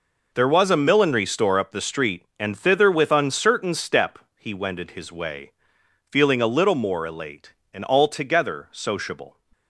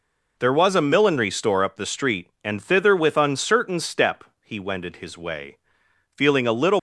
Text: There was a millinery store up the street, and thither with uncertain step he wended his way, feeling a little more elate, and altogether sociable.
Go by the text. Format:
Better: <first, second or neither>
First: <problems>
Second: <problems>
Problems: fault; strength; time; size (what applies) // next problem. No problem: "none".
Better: first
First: pauses between "step" and "he"; slight; at 4.1 s; 0.18 s long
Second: pauses between "step" and "he"; slight; at 4.2 s; 0.18 s long // stops before "more elate and altogether sociable"; at 6.7 s